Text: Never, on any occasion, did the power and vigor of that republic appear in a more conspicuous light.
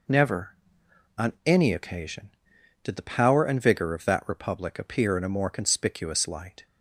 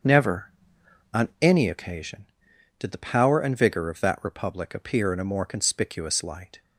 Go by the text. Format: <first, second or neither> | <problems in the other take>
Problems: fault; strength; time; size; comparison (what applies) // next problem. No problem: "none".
first | starts louder than the rest; until 1.6 s; 7 dB